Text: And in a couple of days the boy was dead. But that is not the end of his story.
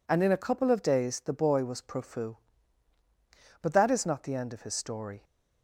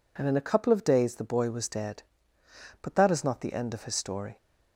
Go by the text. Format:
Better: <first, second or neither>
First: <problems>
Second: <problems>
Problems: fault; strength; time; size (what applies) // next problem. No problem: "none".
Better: second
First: says "profu" for "dead"; at 1.8 s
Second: none